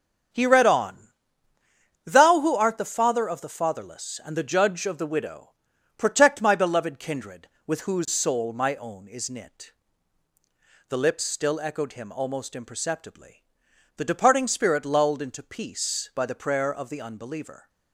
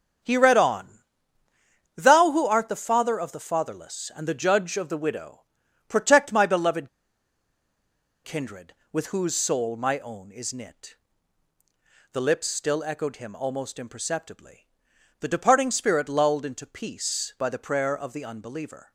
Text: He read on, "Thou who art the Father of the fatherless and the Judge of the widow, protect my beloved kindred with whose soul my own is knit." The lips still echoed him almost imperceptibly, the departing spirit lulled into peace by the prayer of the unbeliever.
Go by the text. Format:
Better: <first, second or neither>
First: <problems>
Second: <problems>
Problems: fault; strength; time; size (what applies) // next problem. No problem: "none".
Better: first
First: starts louder than the rest; strong; until 2.2 s; 7.5 dB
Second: starts louder than the rest; strong; until 2.1 s; 7.5 dB // pauses between "beloved" and "kindred"; strong; at 6.8 s; 1.3 s long